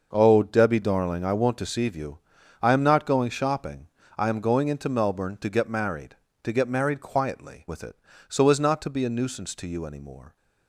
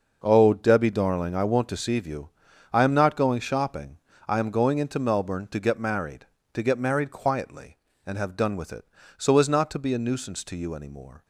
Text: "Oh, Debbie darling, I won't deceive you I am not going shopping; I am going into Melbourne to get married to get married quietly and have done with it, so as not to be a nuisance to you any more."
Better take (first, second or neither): second